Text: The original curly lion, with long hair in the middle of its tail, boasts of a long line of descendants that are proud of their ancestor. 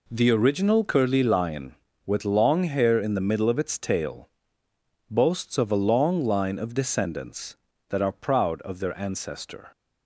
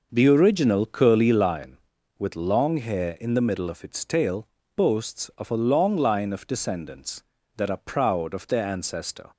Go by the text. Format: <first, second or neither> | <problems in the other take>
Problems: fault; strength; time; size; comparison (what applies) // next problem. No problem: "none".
first | starts louder than the rest; noticeable; until 1.5 s; 5.5 dB